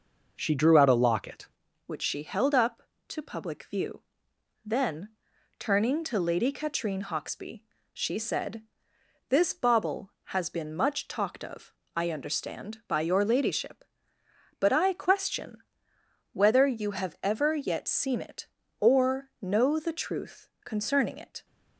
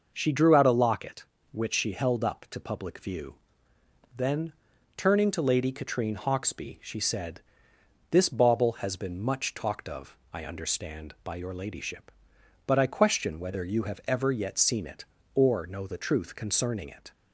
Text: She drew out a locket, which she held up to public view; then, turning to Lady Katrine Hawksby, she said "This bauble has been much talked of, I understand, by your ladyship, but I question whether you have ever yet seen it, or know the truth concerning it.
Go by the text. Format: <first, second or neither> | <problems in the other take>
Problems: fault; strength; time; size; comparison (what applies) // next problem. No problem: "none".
second | changes voice at "which"; from 1.8 s on; 19.6 s long // pauses between "said" and "This"; noticeable; at 8.6 s; 0.66 s long; noticeable in the second // pauses between "question" and "whether"; noticeable; at 15.6 s; 0.70 s long // pauses between "truth" and "concerning"; slight; at 20.4 s; 0.16 s long